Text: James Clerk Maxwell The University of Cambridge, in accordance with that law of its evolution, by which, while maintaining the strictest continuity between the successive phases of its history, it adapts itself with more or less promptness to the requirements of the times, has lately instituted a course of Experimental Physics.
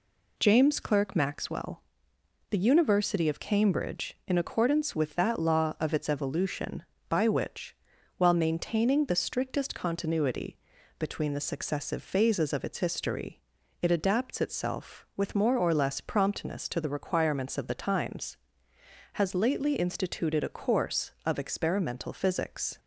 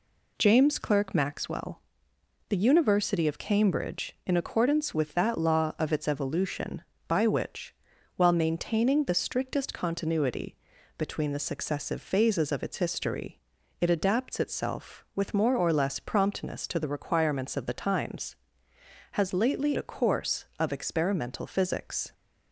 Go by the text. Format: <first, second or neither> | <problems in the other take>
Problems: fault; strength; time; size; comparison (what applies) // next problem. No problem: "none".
first | pauses between "Maxwell" and "The"; noticeable; at 1.7 s; 0.70 s long; noticeable in the first // pauses between "continuity" and "between"; at 10.5 s; 0.40 s long; also in the first // skips "instituted"; at 19.7 s